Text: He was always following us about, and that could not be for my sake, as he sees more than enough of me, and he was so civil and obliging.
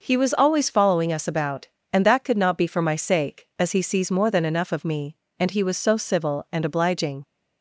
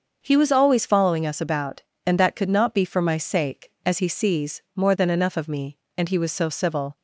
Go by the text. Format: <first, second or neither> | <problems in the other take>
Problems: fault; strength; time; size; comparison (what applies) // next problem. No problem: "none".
first | starts louder than the rest; until 1.2 s; 6.5 dB // stops before "and obliging"; at 6.9 s